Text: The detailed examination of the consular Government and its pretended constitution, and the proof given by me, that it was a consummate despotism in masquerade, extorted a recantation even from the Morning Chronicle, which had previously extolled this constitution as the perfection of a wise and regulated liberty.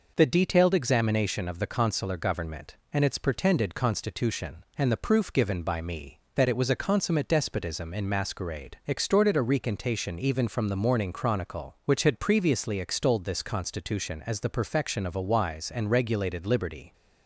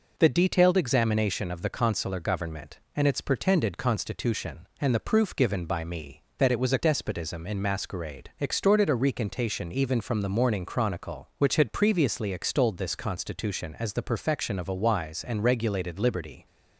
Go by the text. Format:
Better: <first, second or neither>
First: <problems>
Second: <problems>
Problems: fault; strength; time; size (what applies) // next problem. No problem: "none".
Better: first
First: none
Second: skips "consummate"; at 6.7 s